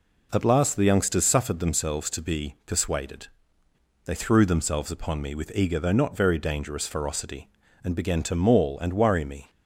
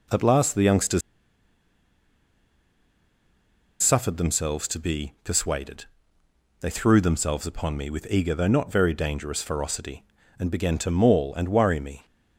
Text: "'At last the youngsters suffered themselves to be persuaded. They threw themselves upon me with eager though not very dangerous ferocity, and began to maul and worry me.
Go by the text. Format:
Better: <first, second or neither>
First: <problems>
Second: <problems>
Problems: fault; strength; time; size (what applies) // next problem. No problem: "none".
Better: first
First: none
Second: pauses between "youngsters" and "suffered"; strong; at 1.0 s; 2.8 s long